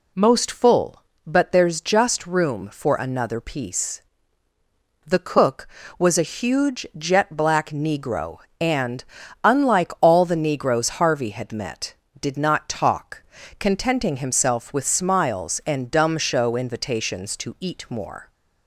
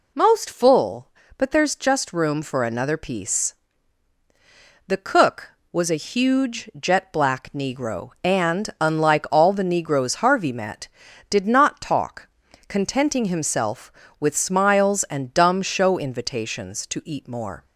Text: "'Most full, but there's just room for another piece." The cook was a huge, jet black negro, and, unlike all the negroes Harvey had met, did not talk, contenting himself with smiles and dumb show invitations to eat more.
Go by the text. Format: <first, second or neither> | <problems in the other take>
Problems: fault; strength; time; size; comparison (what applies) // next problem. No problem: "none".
first | skips "had"; at 10.5 s